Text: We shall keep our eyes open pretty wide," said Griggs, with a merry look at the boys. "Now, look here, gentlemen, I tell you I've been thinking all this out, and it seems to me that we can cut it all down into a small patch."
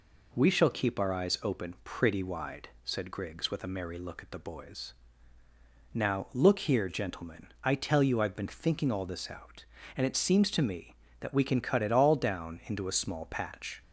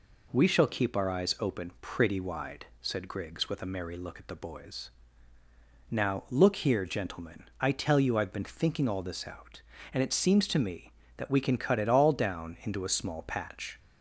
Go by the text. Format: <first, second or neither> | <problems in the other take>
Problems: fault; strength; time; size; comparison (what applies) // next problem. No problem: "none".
neither | none